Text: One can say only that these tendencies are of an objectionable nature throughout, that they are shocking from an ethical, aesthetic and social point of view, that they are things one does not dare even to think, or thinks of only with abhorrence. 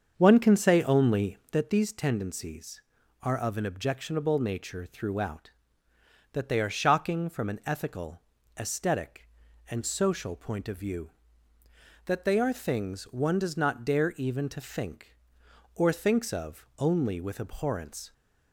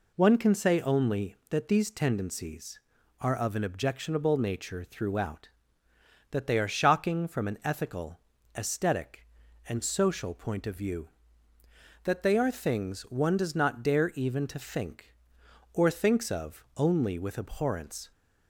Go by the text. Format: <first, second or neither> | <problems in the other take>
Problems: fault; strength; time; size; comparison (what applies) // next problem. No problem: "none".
second | starts louder than the rest; until 1.7 s; 7 dB